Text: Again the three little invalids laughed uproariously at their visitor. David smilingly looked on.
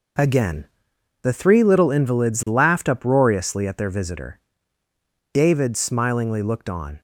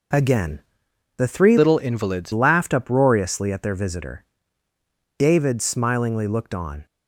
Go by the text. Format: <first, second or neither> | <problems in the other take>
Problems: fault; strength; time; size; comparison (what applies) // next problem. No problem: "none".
first | pauses between "Again" and "the"; noticeable; at 0.5 s; 0.58 s long; noticeable in the first // changes voice from "little" to "invalids"; from 1.5 to 2.3 s; 0.8 s long